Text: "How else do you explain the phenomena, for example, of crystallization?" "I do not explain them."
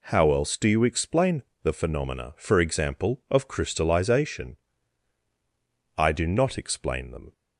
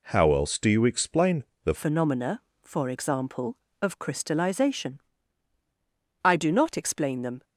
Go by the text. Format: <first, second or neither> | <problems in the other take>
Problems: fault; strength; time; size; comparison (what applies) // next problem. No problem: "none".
first | pauses between "explain" and "the"; slight; at 1.4 s; 0.20 s long; slight in the first // changes voice at "phenomena"; from 1.7 s on; 5.7 s long